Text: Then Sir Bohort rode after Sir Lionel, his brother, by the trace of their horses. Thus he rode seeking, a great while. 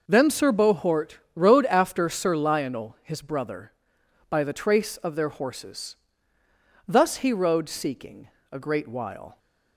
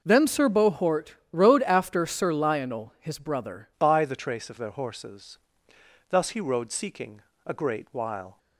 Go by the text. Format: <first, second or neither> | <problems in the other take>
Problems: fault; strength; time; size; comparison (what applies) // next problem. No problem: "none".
first | pauses between "Bohort" and "rode"; slight; at 1.1 s; 0.18 s long; slight in the first // changes voice at "by"; from 3.7 s on; 4.6 s long